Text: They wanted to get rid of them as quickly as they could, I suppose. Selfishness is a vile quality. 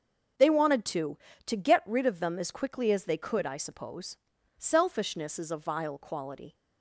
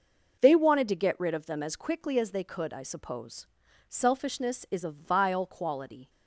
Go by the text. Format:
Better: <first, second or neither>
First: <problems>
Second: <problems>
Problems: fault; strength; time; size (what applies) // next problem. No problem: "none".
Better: second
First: starts louder than the rest; noticeable; until 1.7 s; 6 dB // says "to" twice; at 1.4 s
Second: none